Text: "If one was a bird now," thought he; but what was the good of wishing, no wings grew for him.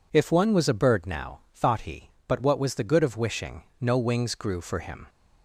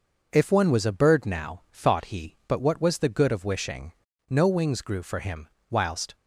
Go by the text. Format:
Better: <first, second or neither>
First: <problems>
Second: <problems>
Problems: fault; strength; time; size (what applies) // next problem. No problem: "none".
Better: first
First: none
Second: goes on to say "Whilst"; slight; from 5.6 s on; 0.46 s long